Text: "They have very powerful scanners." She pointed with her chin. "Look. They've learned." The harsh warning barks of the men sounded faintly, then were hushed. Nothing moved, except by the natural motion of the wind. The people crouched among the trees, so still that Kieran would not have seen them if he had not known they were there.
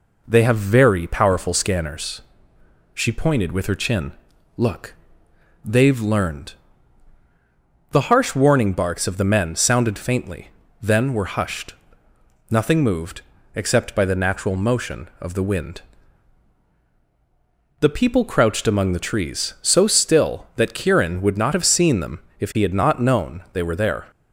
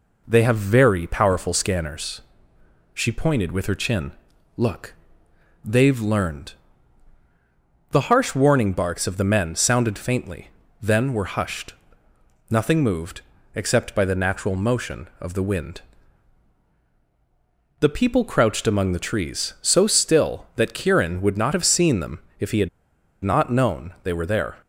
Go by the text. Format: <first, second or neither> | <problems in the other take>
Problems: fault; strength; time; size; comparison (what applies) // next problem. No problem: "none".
first | pauses between "them" and "if"; slight; at 22.1 s; 0.18 s long; slight in the first // pauses between "had" and "not"; noticeable; at 22.6 s; 0.55 s long